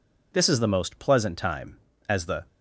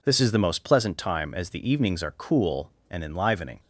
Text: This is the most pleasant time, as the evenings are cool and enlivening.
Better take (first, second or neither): second